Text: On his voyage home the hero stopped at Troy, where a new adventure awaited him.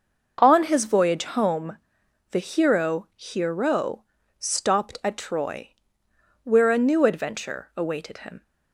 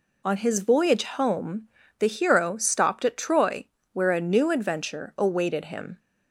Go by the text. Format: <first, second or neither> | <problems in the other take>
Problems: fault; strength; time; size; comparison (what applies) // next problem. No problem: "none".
second | pauses between "home" and "the"; noticeable; at 1.7 s; 0.54 s long; slight in the second // says "hero" twice; at 3.1 s